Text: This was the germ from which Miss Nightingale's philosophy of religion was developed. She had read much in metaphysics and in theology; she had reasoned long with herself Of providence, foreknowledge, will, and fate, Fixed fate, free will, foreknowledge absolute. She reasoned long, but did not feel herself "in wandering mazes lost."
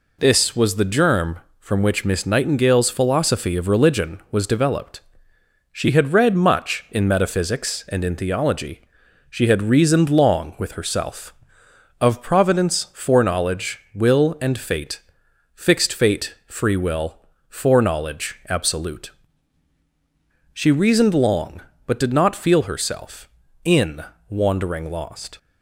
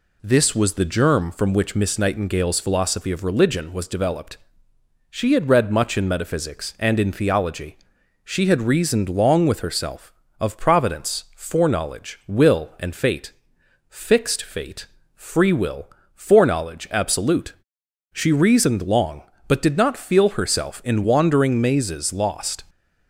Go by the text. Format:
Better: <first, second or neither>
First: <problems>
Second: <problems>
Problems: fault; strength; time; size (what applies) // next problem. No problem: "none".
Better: second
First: pauses between "in" and "wandering"; slight; at 24.0 s; 0.28 s long // skips "mazes"; at 24.8 s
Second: none